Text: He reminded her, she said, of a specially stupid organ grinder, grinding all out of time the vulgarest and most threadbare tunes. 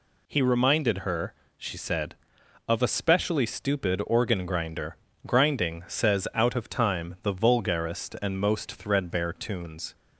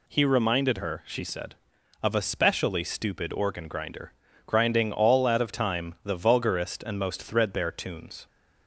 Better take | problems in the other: second | says "says" for "all"; at 5.8 s

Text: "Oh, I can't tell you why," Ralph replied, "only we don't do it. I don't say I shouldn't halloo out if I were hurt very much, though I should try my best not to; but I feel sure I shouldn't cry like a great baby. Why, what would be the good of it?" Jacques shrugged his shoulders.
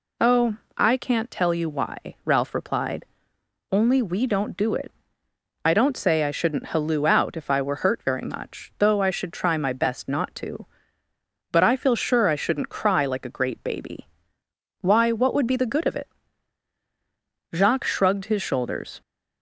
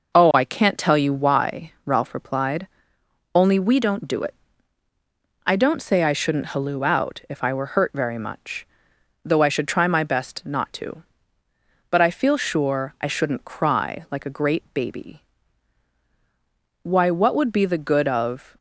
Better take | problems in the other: first | stops before "it Jacques shrugged his shoulders"; at 18.5 s

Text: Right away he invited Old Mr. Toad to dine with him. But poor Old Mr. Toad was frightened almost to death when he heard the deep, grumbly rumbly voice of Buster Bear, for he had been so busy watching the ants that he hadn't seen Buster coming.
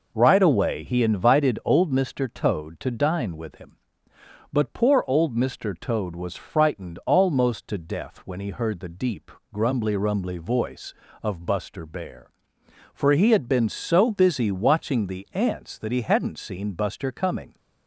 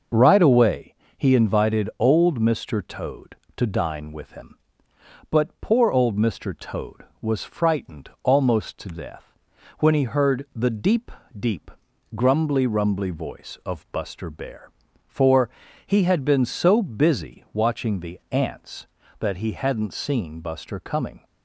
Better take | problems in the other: first | starts louder than the rest; noticeable; until 1.3 s; 6 dB // pauses between "away" and "he"; slight; at 0.9 s; 0.24 s long // pauses between "death" and "when"; noticeable; at 9.2 s; 0.56 s long // says "deep" twice; at 11.3 s // pauses between "for" and "he"; at 15.4 s; 0.38 s long

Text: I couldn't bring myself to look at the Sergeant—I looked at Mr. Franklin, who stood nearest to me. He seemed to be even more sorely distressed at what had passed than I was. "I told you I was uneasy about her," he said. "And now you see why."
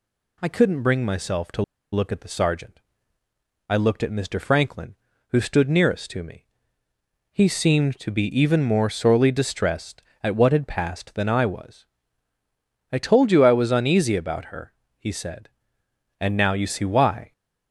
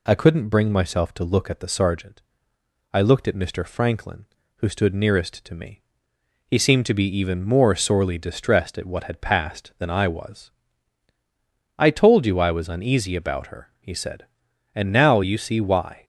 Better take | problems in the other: second | pauses between "to" and "look"; slight; at 1.6 s; 0.30 s long

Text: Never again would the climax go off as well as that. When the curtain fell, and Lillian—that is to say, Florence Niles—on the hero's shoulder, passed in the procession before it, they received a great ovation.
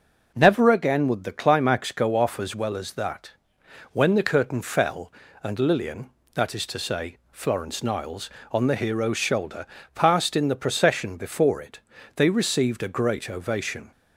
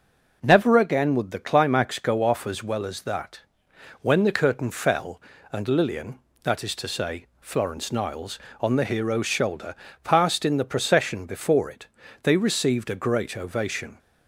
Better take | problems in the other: neither | none

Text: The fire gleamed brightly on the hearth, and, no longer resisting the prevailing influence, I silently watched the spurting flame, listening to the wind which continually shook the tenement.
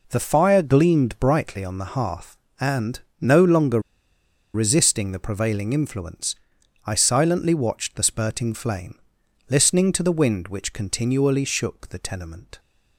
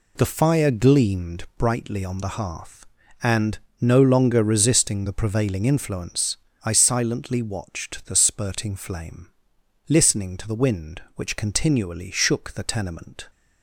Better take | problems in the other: second | pauses between "longer" and "resisting"; noticeable; at 3.7 s; 0.74 s long

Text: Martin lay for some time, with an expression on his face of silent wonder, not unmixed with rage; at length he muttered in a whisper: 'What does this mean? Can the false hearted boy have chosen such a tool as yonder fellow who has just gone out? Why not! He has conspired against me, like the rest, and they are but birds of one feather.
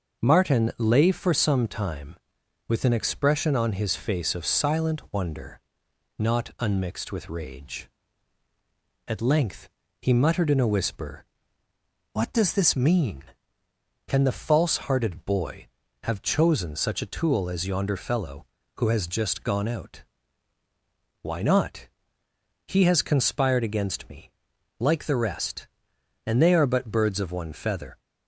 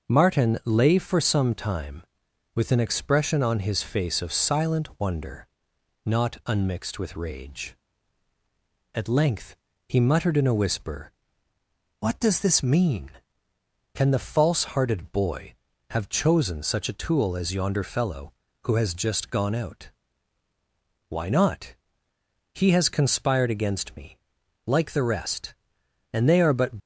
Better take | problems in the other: first | pauses between "length" and "he"; slight; at 9.5 s; 0.32 s long; slight in the first // stops before "birds of one feather"; at 26.7 s

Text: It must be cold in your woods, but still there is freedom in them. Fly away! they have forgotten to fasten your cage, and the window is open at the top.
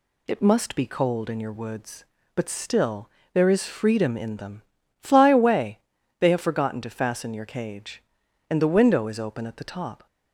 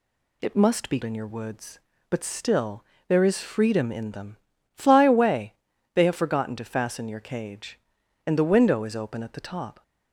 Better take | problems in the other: first | skips "cold"; at 1.0 s // pauses between "still" and "there"; slight; at 2.8 s; 0.24 s long; slight in the first

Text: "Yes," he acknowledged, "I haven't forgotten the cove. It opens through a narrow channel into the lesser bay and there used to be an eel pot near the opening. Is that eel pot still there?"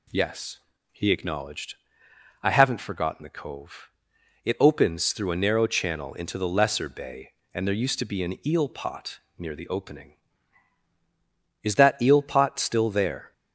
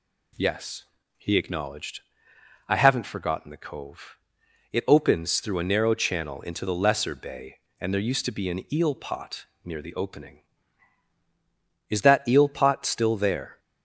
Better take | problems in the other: neither | pauses between "pot" and "near"; slight; the same in both

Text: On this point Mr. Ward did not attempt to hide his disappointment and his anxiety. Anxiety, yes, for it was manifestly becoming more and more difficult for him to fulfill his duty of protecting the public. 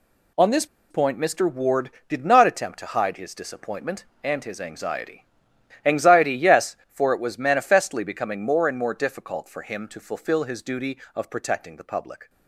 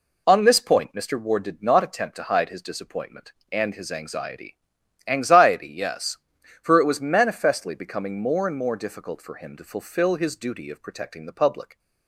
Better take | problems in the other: second | pauses between "this" and "point"; slight; at 0.6 s; 0.25 s long

